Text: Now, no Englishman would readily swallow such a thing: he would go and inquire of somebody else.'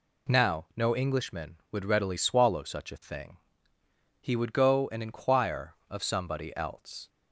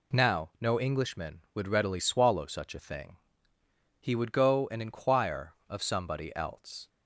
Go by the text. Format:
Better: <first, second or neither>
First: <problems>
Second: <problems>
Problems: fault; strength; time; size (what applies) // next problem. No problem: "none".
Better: neither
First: none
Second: none